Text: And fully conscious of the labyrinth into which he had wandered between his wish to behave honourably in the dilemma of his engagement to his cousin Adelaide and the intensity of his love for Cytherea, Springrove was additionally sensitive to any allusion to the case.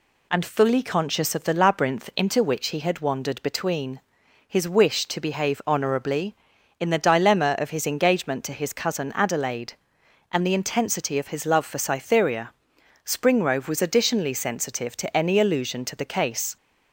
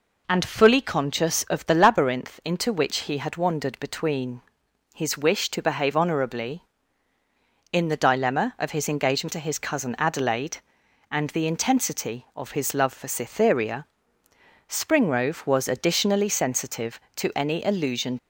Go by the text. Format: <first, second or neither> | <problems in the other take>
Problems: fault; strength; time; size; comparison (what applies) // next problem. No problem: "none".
first | pauses between "between" and "his"; noticeable; at 4.4 s; 0.54 s long; noticeable in the first // stops before "to the case"; at 18.1 s